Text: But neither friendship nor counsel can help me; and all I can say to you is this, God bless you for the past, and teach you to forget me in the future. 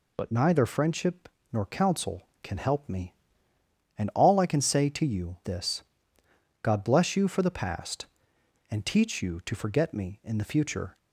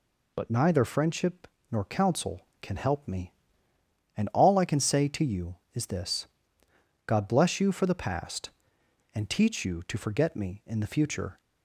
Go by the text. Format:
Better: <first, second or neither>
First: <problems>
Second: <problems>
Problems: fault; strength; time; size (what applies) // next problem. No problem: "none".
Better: second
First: pauses between "friendship" and "nor"; slight; at 1.2 s; 0.24 s long // skips "is"; at 5.4 s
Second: pauses between "friendship" and "nor"; slight; at 1.4 s; 0.24 s long